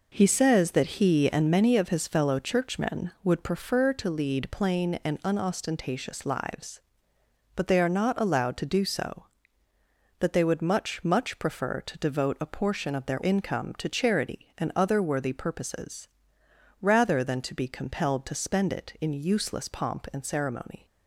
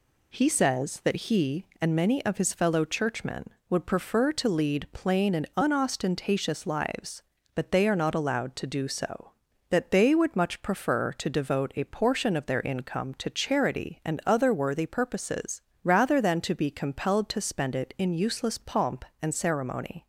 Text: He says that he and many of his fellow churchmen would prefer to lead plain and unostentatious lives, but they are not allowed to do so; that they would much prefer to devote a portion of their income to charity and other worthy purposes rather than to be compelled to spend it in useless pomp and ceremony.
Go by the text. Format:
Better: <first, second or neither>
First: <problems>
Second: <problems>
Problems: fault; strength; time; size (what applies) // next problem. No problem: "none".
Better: second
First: says "much" twice; at 11.0 s // pauses between "purposes" and "rather"; noticeable; at 16.0 s; 0.72 s long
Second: pauses between "purposes" and "rather"; slight; at 15.6 s; 0.24 s long